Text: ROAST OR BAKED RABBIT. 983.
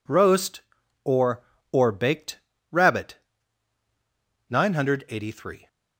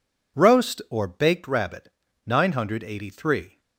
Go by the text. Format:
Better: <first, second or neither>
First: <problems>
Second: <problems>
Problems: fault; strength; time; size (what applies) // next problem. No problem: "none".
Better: second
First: says "OR" twice; at 1.7 s // pauses between "BAKED" and "RABBIT"; slight; at 2.3 s; 0.32 s long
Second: none